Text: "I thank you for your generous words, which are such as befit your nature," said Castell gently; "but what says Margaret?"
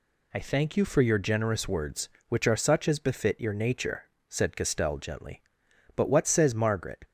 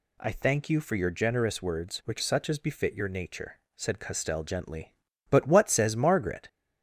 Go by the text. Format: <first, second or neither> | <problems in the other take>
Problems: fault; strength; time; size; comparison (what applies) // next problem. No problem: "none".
first | skips "are"; at 2.2 s